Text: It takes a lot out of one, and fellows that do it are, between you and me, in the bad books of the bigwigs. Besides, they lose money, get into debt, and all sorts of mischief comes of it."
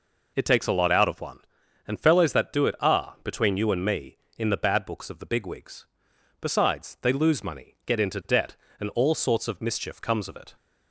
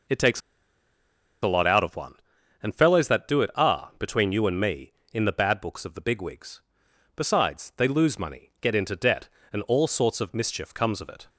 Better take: first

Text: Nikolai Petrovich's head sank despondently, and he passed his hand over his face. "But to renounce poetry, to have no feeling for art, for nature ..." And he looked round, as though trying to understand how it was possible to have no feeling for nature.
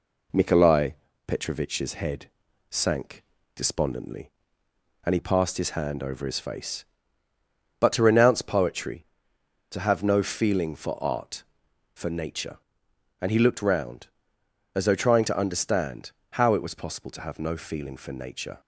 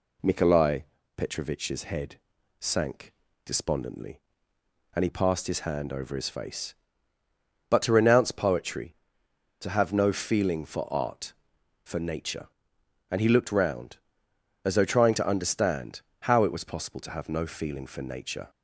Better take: second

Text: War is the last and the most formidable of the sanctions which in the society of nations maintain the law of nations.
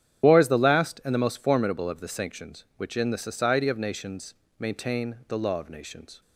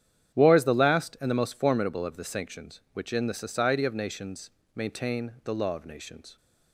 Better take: second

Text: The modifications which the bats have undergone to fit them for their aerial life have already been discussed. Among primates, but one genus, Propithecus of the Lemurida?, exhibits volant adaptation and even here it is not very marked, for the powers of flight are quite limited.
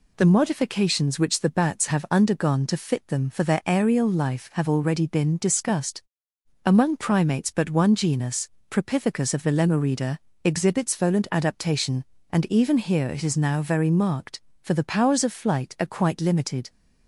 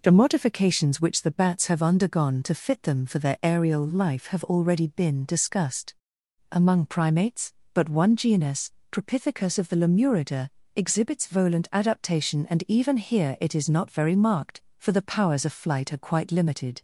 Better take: second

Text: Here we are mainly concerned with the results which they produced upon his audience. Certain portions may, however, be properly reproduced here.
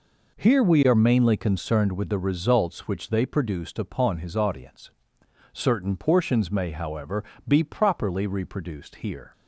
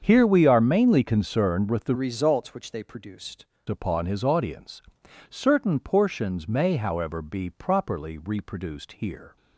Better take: first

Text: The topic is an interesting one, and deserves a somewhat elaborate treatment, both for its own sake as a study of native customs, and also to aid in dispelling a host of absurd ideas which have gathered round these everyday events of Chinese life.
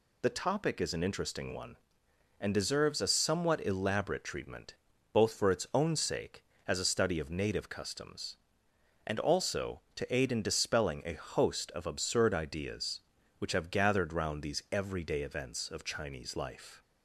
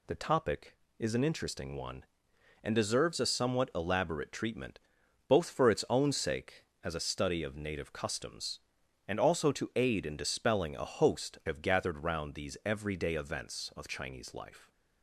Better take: first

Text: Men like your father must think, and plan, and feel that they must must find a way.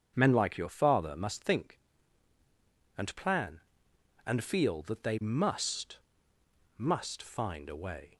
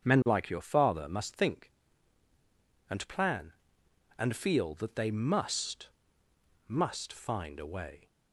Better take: neither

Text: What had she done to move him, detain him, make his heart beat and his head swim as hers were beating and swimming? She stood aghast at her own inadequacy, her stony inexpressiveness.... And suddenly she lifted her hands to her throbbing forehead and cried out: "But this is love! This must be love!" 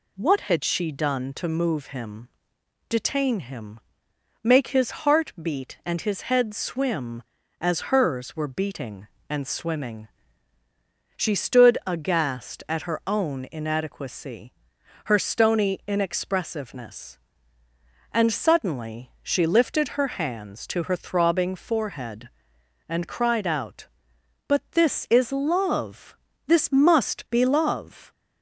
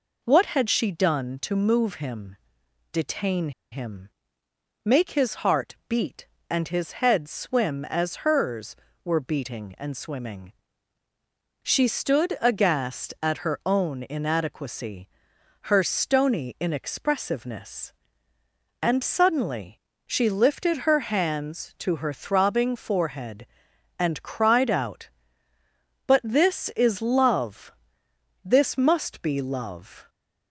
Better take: first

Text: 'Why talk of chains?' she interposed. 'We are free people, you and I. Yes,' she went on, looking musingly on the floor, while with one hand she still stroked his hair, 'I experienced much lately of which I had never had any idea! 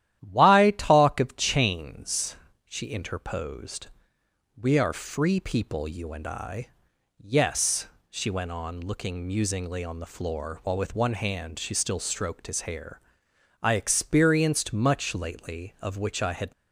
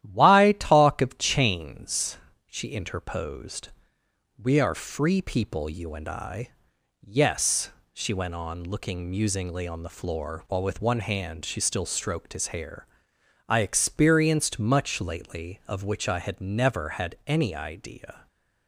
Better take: second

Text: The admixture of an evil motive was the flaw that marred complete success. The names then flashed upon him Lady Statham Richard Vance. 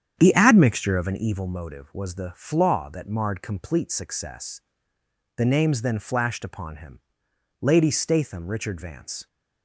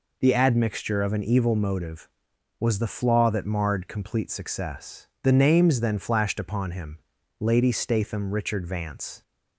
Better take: second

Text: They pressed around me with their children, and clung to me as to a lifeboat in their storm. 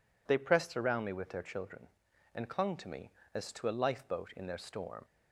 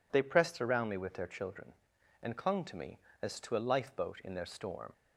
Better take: neither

